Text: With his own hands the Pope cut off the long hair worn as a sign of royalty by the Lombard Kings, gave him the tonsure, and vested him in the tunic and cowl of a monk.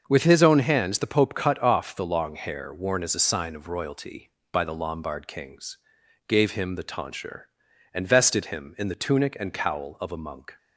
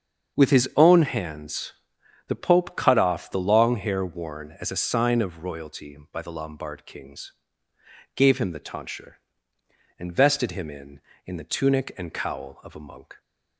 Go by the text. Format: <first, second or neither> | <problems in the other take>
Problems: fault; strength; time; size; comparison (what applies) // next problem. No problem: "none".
first | starts louder than the rest; until 1.4 s; 7 dB; also in the first // pauses between "hands" and "the"; noticeable; at 1.7 s; 0.56 s long // says "in" twice; at 11.2 s